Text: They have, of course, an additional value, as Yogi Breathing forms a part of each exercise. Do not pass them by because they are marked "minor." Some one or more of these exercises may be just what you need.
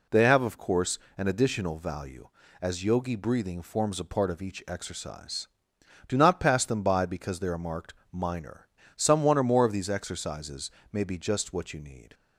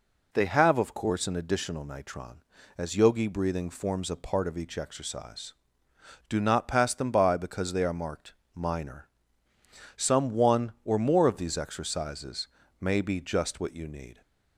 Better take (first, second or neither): first